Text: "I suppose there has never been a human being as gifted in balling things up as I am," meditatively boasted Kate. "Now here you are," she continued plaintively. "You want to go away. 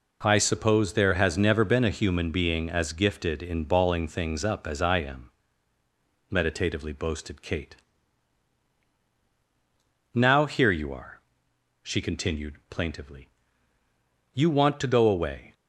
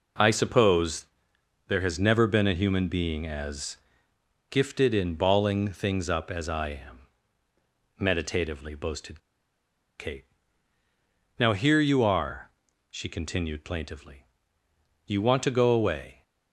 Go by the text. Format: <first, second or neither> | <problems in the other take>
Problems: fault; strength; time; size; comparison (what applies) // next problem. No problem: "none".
first | pauses between "suppose" and "there"; noticeable; at 1.0 s; 0.62 s long // pauses between "as" and "gifted"; noticeable; at 3.7 s; 0.72 s long // pauses between "boasted" and "Kate"; noticeable; at 9.2 s; 0.78 s long